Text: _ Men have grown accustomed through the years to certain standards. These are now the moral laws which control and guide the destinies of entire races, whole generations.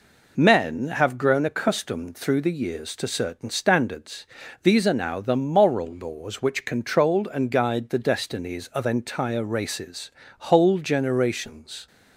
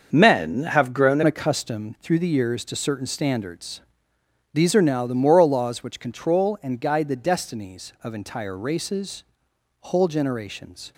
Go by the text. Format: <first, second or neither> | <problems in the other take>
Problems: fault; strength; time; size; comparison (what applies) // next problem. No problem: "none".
first | starts louder than the rest; until 1.1 s; 6.5 dB // changes voice at "accustomed"; from 1.2 s on; 9.7 s long